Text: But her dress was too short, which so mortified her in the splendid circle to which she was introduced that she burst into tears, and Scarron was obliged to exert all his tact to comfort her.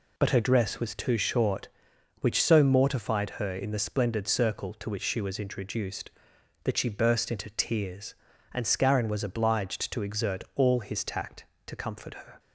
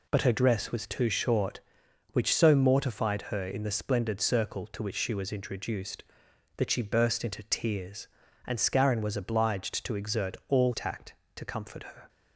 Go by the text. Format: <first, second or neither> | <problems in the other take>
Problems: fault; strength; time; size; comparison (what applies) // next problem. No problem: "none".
first | skips "his"; at 10.7 s